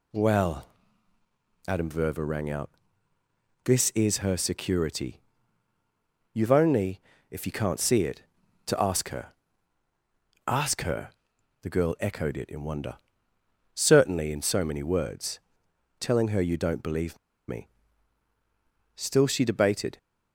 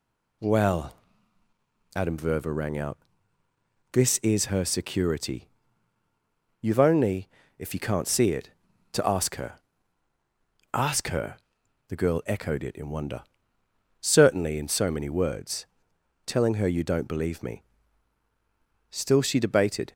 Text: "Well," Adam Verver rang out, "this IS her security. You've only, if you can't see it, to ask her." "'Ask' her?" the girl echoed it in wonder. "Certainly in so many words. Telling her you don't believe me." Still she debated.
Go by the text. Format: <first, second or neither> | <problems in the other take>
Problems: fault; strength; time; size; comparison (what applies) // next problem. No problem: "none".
second | pauses between "believe" and "me"; slight; at 17.1 s; 0.30 s long